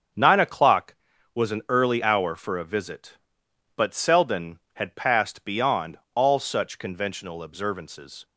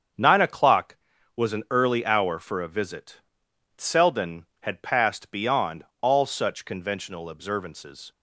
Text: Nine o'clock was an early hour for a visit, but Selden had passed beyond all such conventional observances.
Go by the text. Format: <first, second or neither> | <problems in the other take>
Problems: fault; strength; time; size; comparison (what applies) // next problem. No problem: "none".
first | starts louder than the rest; strong; until 1.5 s; 7.5 dB; strong in the first // skips "but"; at 3.5 s // pauses between "beyond" and "all"; slight; at 5.8 s; 0.18 s long; slight in the first